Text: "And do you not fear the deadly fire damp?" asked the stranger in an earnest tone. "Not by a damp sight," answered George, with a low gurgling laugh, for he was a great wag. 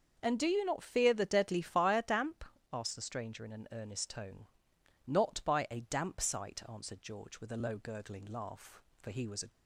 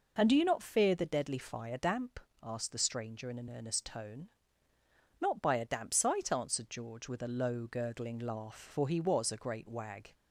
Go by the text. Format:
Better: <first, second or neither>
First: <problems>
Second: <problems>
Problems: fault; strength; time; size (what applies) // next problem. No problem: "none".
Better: second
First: starts louder than the rest; until 1.2 s; 6.5 dB // stops before "great wag"; at 9.5 s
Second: none